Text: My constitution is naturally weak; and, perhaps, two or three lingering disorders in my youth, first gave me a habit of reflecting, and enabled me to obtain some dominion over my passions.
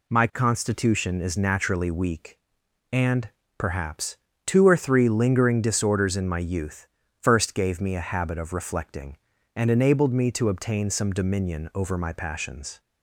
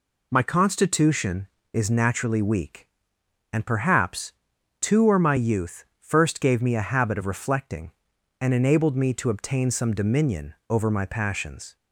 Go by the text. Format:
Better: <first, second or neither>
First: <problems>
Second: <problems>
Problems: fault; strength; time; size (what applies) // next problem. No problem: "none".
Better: first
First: none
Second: skips "three lingering disorders in"; at 5.1 s // pauses between "dominion" and "over"; slight; at 10.5 s; 0.16 s long